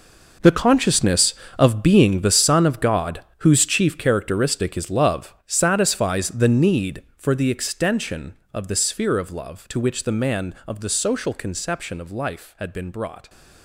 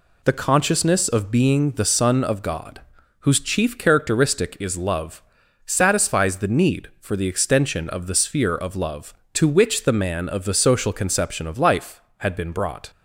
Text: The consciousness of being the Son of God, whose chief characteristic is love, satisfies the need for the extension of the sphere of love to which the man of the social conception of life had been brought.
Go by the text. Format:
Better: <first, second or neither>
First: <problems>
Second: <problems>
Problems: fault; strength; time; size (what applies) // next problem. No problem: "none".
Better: second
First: gets quieter; strong; throughout; 14.5 dB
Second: none